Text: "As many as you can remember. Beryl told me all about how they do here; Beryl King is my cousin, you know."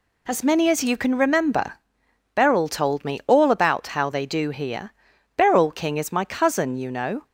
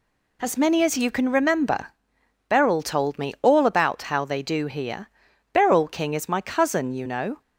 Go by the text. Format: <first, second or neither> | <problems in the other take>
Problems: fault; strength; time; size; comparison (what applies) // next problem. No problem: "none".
neither | none